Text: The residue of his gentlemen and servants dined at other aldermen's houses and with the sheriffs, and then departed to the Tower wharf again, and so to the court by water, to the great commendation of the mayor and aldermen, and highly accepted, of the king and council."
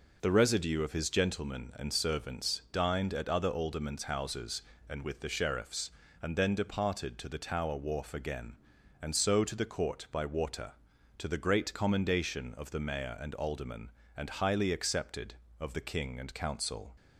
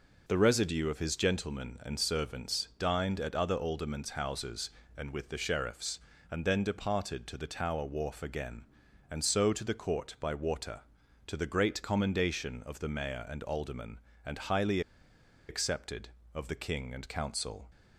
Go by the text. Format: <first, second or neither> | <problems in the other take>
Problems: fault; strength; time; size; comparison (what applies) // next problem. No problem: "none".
first | pauses between "highly" and "accepted"; noticeable; at 14.8 s; 0.68 s long